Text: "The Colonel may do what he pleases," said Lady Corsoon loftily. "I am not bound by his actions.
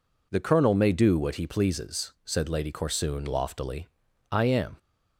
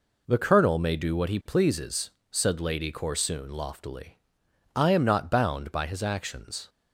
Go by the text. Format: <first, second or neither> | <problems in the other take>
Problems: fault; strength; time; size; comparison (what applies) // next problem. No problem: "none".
second | stops before "not bound by his actions"; at 4.7 s